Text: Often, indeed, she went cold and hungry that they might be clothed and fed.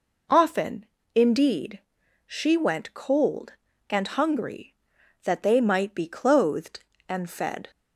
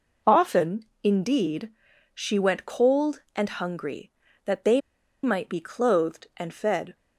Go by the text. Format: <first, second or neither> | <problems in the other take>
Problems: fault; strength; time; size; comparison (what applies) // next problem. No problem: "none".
first | pauses between "they" and "might"; at 4.7 s; 0.43 s long